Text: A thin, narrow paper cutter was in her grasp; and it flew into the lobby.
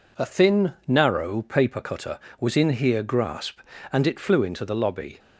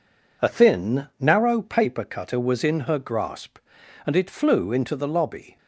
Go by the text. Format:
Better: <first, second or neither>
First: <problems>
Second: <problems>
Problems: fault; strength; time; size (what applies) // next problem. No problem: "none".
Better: second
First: says "here" for "her"; at 2.6 s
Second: none